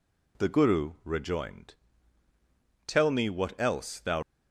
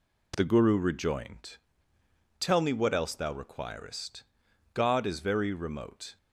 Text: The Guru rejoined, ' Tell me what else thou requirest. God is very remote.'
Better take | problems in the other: second | stops before "requirest God is very remote"; at 4.2 s

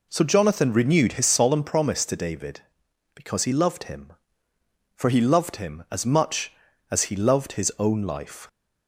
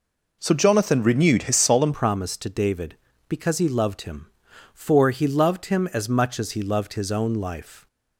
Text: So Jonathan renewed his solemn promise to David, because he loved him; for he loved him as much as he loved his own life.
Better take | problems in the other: first | changes voice at "promise"; from 1.9 s on; 5.9 s long

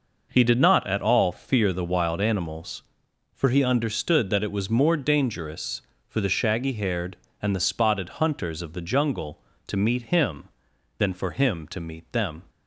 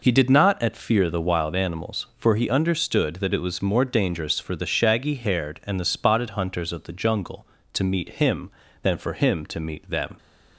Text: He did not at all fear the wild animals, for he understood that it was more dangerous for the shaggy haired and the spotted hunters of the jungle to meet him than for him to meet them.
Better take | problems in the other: first | skips "all"; at 0.7 s

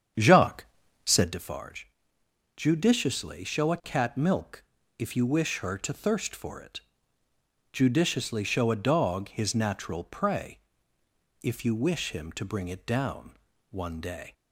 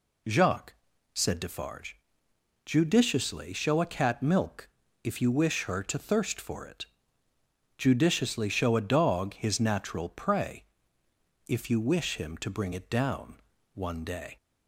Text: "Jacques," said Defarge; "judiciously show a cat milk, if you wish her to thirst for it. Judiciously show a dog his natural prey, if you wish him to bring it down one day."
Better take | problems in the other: second | starts louder than the rest; strong; until 1.3 s; 8 dB // pauses between "down" and "one"; slight; at 13.3 s; 0.32 s long; slight in the second

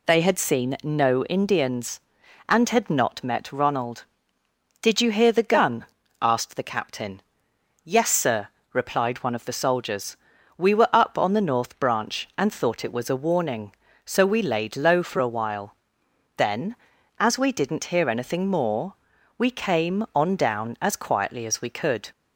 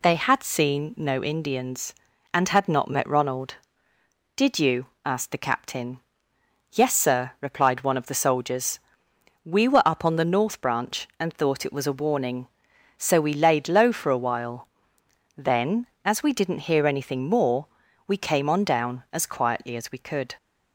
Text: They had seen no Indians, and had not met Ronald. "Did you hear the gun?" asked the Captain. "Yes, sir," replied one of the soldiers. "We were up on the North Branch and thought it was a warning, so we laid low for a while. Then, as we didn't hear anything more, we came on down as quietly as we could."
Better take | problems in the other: first | skips "hear the gun"; at 4.9 s

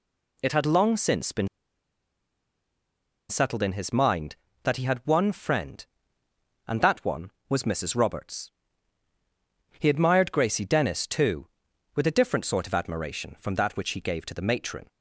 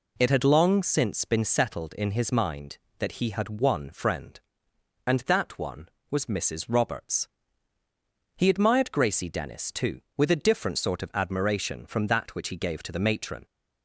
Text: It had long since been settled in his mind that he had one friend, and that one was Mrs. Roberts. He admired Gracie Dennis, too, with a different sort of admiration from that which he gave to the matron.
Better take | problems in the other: second | pauses between "been" and "settled"; strong; at 1.4 s; 1.8 s long

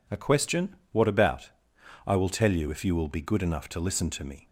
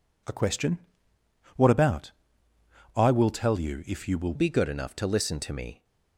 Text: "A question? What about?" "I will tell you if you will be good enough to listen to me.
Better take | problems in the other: first | changes voice at "be"; from 4.3 s on; 1.5 s long

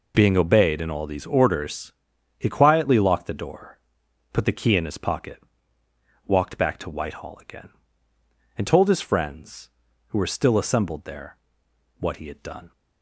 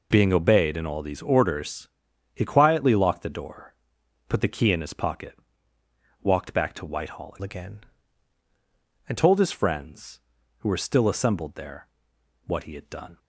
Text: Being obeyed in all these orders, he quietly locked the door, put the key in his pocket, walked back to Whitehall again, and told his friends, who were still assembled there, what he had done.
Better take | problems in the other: first | changes voice from "again" to "and"; from 7.4 to 9.1 s; 1.7 s long

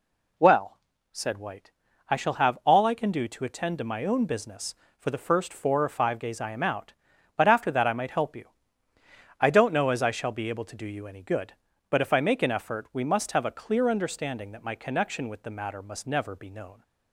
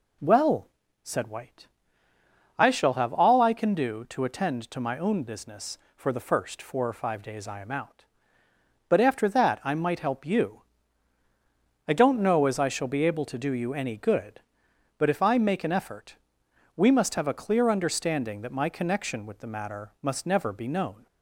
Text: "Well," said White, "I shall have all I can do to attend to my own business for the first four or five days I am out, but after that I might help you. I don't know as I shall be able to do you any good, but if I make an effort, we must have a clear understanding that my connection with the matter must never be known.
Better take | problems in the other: neither | none

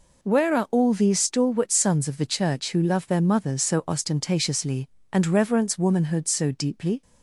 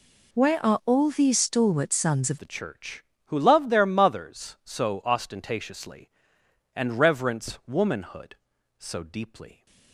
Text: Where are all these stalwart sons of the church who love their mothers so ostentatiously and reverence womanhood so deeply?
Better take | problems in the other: first | changes voice at "the"; from 2.3 s on; 7.3 s long

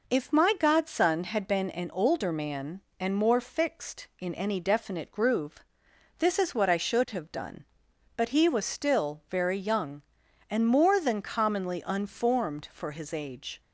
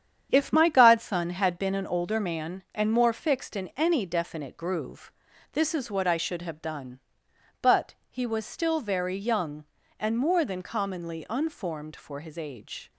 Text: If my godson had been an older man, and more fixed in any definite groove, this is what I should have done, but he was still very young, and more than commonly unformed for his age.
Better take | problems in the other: first | gets quieter; strong; throughout; 7 dB

